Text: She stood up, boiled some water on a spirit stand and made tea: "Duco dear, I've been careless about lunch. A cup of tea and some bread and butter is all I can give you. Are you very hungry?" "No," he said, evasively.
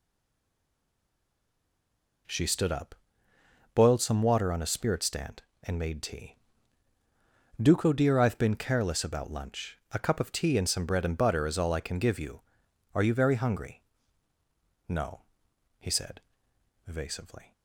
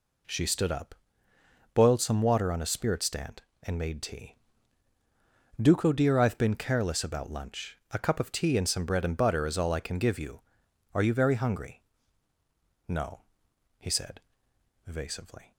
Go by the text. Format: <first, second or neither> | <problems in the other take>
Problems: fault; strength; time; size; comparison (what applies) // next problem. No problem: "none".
second | stays silent before the first word; until 2.2 s; 2.2 s long